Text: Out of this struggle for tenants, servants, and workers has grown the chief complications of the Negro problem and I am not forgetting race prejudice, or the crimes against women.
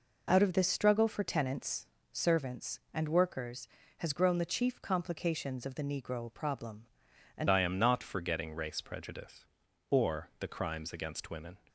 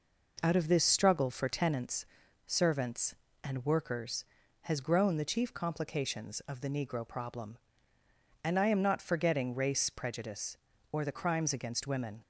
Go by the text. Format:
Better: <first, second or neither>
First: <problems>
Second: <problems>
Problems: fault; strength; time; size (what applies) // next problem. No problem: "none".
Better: second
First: changes voice at "I"; from 7.5 s on; 4.0 s long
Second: none